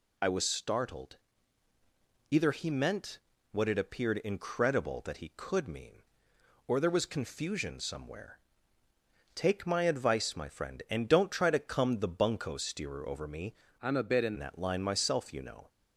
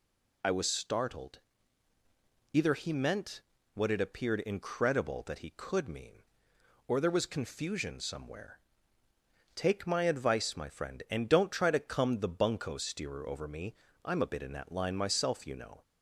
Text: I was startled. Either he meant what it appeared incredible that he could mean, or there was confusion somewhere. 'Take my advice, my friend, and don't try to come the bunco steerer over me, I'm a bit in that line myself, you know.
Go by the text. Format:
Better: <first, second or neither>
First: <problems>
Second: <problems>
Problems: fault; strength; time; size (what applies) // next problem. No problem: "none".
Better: second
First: pauses between "meant" and "what"; slight; at 3.1 s; 0.32 s long // changes voice from "I'm" to "in"; from 13.8 to 14.3 s; 0.5 s long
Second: pauses between "meant" and "what"; slight; at 3.4 s; 0.32 s long